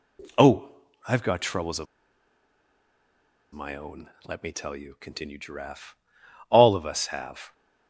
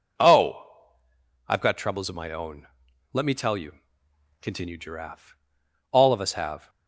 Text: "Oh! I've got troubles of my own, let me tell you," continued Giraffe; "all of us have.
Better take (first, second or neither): second